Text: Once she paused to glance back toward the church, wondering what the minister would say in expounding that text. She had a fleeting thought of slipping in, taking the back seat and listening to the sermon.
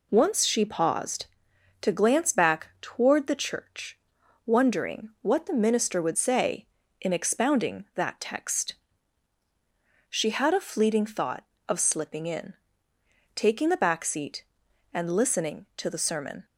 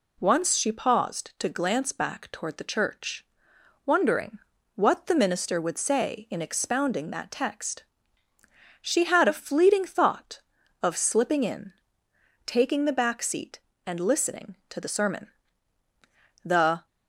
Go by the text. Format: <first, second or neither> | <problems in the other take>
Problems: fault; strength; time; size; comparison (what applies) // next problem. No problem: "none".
first | pauses between "wondering" and "what"; slight; at 4.3 s; 0.36 s long // goes on to say "The"; slight; from 16.4 s on; 0.42 s long